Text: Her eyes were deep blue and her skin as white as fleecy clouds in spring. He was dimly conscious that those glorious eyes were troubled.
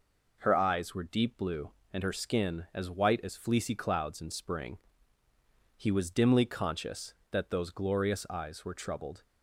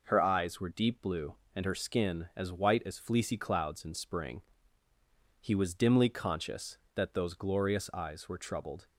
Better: neither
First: none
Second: none

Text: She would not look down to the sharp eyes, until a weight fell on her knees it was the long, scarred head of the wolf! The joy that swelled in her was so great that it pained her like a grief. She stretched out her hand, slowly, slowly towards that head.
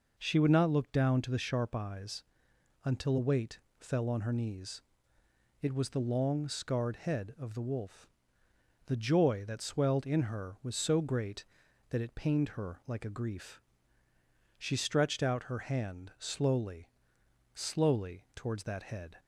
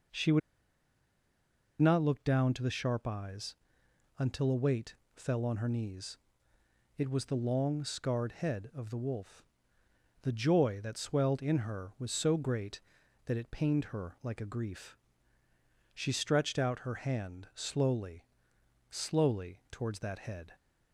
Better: first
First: pauses between "weight" and "fell"; slight; at 3.5 s; 0.22 s long // pauses between "knees" and "it"; noticeable; at 4.8 s; 0.78 s long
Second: pauses between "would" and "not"; strong; at 0.4 s; 1.4 s long // pauses between "weight" and "fell"; slight; at 4.9 s; 0.22 s long // pauses between "knees" and "it"; noticeable; at 6.1 s; 0.78 s long

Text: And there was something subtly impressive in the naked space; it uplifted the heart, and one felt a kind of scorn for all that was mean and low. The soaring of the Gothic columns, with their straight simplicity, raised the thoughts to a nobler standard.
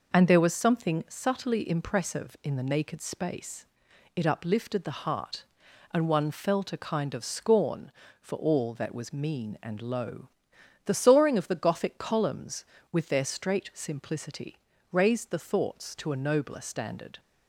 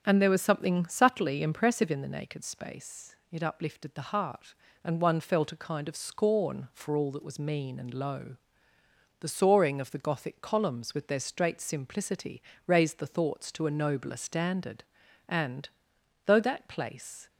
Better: first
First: none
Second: starts louder than the rest; strong; until 1.0 s; 7.5 dB // goes on to say "And though that place"; strong; from 15.2 s on; 2.0 s long

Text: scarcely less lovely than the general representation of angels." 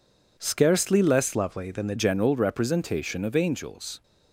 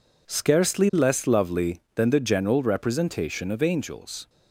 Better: second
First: changes voice from "lovely" to "the"; from 1.3 to 1.9 s; 0.6 s long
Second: none

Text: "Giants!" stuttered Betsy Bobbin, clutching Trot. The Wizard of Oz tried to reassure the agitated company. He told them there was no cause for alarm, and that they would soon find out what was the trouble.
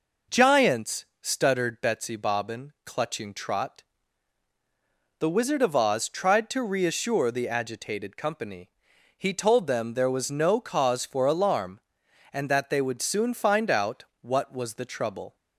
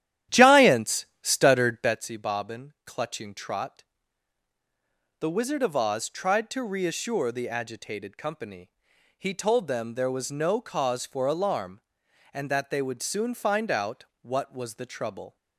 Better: first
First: pauses between "out" and "what"; slight; at 14.0 s; 0.18 s long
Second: starts louder than the rest; strong; until 2.1 s; 12 dB // pauses between "out" and "what"; slight; at 14.0 s; 0.18 s long

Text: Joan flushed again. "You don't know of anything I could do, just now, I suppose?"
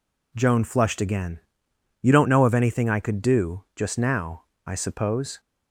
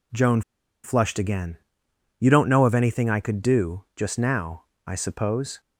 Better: first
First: none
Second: pauses between "Joan" and "flushed"; at 0.4 s; 0.41 s long

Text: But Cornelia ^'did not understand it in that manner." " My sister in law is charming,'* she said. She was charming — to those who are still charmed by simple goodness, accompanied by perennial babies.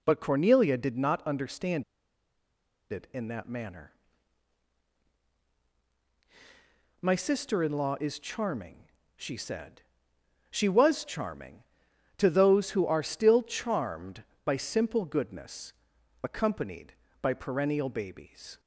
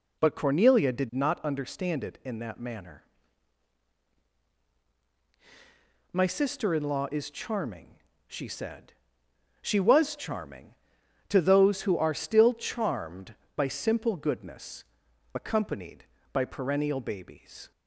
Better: second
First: pauses between "understand" and "it"; at 1.8 s; 1.0 s long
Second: none

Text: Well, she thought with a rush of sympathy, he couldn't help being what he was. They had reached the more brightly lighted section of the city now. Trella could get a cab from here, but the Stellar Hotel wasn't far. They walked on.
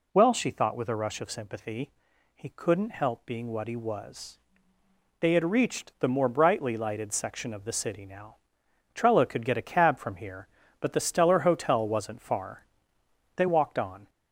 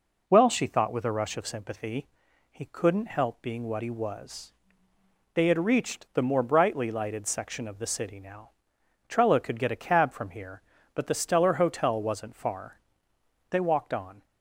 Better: second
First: gets louder; slight; throughout; 2.5 dB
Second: none

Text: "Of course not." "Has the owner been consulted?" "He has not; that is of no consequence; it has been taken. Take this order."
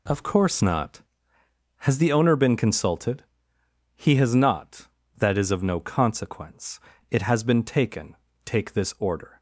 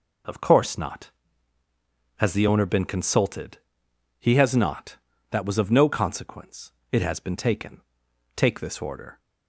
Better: first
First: none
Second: says "was" for "is"; at 5.4 s

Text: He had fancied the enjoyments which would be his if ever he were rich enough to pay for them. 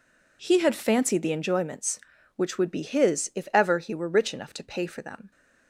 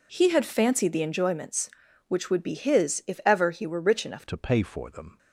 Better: first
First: none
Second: changes voice at "to"; from 4.2 s on; 0.9 s long

